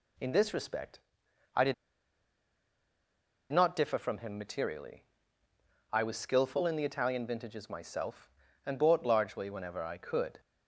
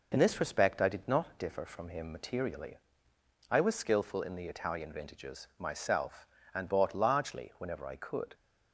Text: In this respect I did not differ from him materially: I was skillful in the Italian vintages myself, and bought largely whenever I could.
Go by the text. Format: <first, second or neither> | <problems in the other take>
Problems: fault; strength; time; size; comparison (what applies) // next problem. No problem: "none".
second | pauses between "respect" and "I"; noticeable; at 0.9 s; 0.56 s long // pauses between "did" and "not"; strong; at 1.7 s; 1.7 s long